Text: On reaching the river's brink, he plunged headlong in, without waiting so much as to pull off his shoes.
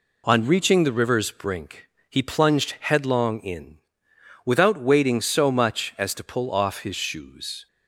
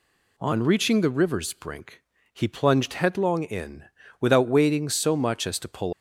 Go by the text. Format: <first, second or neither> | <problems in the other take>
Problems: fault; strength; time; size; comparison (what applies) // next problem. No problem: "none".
first | stops before "off his shoes"; at 5.9 s